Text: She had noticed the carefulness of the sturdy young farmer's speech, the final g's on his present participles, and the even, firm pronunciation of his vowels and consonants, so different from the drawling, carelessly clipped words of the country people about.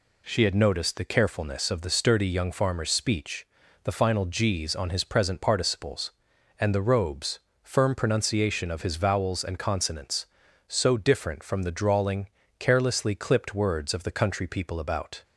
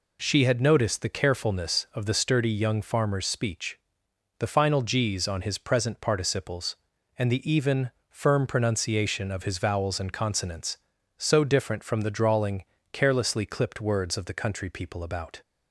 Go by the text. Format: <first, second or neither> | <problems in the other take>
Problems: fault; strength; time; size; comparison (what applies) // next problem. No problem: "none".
second | says "robes" for "even"; at 6.8 s